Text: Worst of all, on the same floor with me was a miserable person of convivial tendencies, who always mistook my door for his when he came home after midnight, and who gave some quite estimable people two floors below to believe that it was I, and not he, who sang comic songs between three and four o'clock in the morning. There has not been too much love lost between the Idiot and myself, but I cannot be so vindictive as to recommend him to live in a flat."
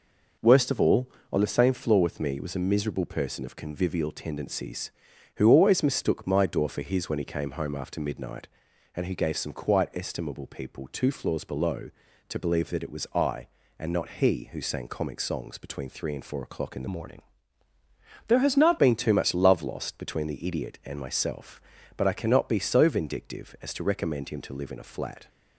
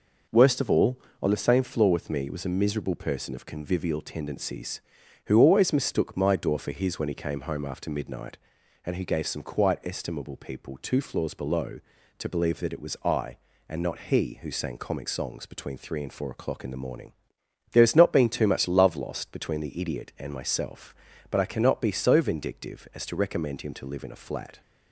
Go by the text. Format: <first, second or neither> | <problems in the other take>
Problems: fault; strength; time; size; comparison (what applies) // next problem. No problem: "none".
second | changes voice from "morning" to "not"; from 16.8 to 18.7 s; 1.9 s long